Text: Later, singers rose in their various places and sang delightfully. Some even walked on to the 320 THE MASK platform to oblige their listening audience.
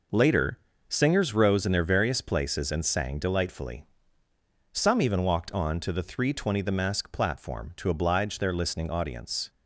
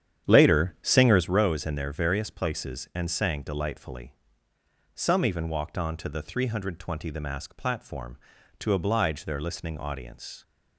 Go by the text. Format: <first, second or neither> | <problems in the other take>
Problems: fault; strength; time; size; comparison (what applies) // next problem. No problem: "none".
first | starts louder than the rest; strong; until 1.4 s; 9.5 dB